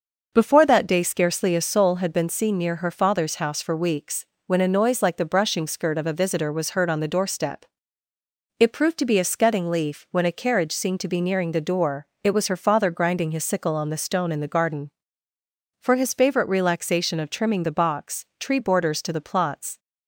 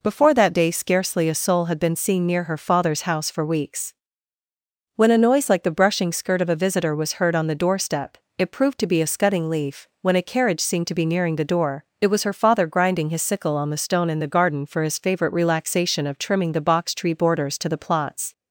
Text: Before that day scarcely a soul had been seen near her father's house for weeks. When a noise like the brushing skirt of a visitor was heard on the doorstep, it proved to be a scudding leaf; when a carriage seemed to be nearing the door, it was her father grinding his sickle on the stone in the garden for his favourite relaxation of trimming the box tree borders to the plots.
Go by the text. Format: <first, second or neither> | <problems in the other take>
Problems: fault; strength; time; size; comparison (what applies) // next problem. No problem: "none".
neither | none